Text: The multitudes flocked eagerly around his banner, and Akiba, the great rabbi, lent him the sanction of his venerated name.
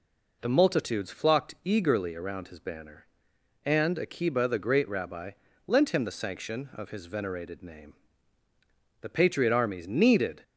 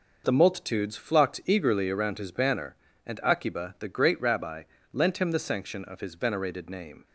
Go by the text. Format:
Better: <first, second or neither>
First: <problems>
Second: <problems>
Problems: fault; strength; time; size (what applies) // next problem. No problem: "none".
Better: second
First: goes on to say "The patriot armies needed"; from 9.0 s on; 1.4 s long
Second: none